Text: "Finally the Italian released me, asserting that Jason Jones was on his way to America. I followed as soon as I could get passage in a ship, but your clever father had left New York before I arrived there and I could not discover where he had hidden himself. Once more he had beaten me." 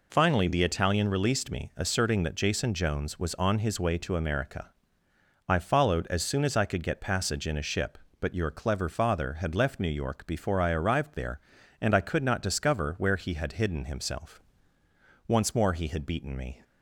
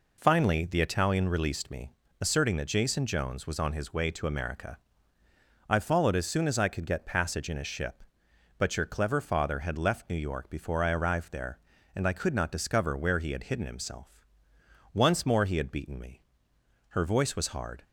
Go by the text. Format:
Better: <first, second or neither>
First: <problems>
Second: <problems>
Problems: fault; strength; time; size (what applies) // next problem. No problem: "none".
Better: first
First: none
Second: goes on to say "Her voice was hard"; noticeable; from 16.9 s on; 0.92 s long